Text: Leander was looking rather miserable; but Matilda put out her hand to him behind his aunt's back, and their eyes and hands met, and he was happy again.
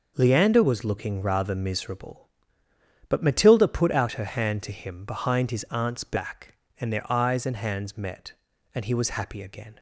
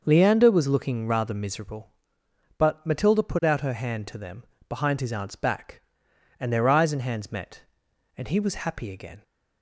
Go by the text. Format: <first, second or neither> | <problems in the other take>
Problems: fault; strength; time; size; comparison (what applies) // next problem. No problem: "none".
first | starts louder than the rest; noticeable; until 1.0 s; 6 dB // says "them" for "him"; at 4.1 s